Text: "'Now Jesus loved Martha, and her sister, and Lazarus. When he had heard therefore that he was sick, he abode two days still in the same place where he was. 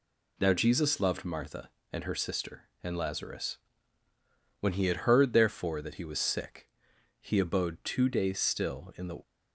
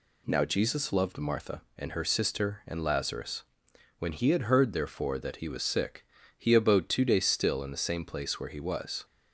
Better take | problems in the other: second | stops before "same place where he was"; at 9.2 s

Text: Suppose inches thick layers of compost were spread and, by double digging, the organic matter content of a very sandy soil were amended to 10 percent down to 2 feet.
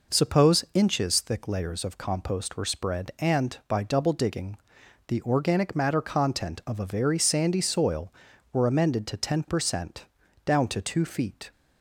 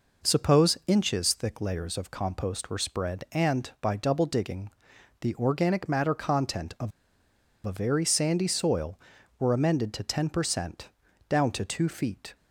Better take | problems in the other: first | pauses between "of" and "a"; noticeable; at 6.9 s; 0.75 s long // pauses between "percent" and "down"; at 10.8 s; 0.40 s long; also in the first

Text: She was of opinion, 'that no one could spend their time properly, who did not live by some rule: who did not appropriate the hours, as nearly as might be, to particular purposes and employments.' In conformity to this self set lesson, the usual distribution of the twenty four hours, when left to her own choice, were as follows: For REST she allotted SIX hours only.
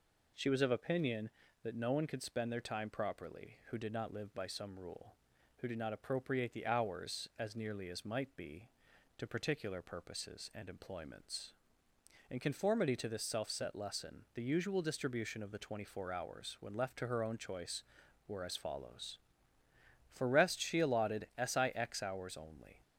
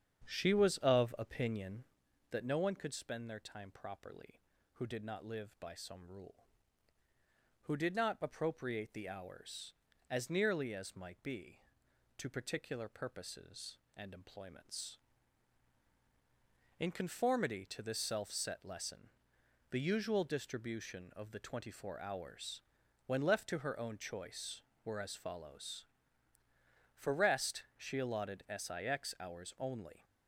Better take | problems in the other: first | starts louder than the rest; strong; until 2.1 s; 8 dB

